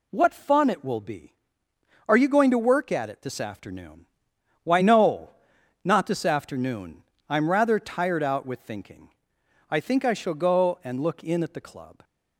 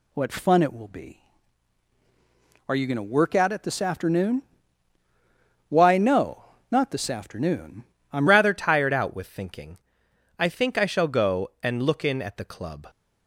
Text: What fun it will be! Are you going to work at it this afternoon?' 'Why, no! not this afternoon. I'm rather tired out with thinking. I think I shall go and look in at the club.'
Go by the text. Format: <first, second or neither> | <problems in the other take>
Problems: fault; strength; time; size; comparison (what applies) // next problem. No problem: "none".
first | changes voice at "rather"; from 8.2 s on; 4.6 s long